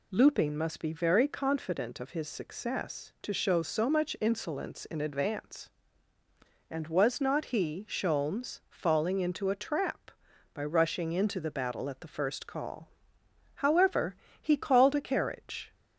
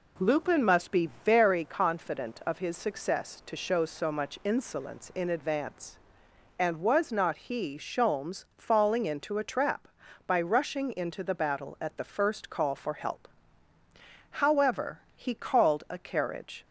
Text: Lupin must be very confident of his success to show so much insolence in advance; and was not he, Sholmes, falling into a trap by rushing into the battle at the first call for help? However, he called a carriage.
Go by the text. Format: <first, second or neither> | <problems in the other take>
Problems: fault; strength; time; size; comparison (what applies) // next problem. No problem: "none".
second | skips "for help"; at 13.2 s